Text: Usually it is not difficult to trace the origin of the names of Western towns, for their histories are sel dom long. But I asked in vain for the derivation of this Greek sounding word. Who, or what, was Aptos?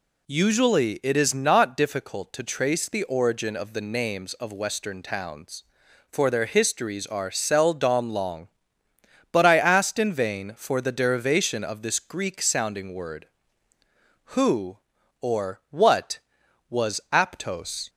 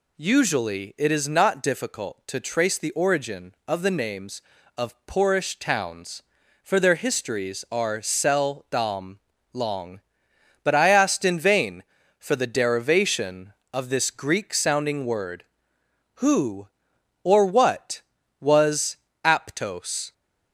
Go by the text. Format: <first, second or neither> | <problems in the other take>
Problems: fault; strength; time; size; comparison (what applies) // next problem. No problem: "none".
first | says "Poorish" for "Western"; at 5.0 s // pauses between "dom" and "long"; slight; at 9.1 s; 0.34 s long // pauses between "was" and "Aptos"; slight; at 18.9 s; 0.28 s long